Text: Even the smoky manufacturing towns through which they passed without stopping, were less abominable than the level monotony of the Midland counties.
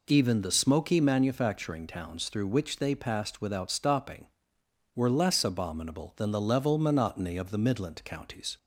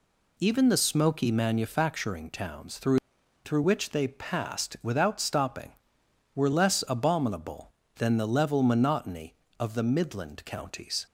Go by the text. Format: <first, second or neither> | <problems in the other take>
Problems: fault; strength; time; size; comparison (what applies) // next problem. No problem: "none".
first | says "through" twice; at 3.4 s